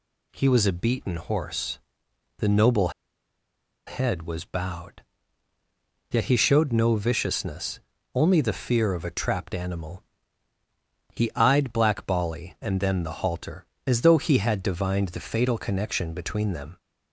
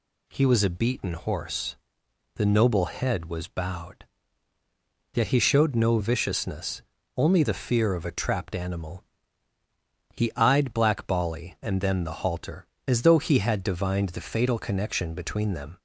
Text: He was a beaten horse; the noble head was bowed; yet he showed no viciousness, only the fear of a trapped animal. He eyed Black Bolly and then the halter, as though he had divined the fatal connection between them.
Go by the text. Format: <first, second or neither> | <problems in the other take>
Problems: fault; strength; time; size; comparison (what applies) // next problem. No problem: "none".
second | pauses between "noble" and "head"; noticeable; at 2.8 s; 0.97 s long